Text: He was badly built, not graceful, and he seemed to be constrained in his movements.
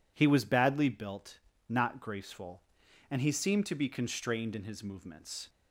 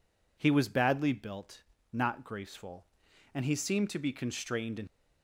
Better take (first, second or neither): first